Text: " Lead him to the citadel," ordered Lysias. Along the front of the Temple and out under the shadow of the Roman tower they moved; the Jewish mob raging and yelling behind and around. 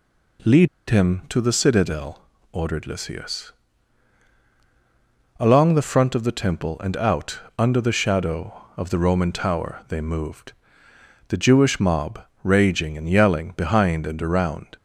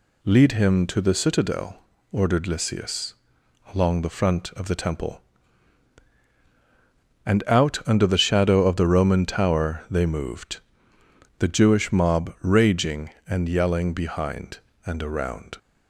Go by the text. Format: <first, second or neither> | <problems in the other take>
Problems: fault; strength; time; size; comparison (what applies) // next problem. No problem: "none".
second | pauses between "Lead" and "him"; slight; at 0.6 s; 0.22 s long // pauses between "out" and "under"; slight; at 7.3 s; 0.20 s long // pauses between "mob" and "raging"; slight; at 12.2 s; 0.18 s long